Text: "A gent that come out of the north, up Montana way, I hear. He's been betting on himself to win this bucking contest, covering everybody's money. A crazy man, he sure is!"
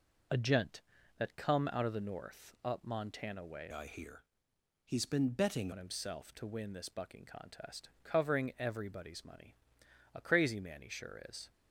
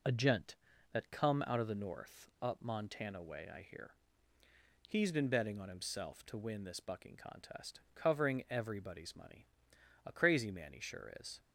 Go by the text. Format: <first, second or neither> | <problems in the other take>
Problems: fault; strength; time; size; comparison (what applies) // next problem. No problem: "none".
second | changes voice from "I" to "betting"; from 3.7 to 5.7 s; 2.0 s long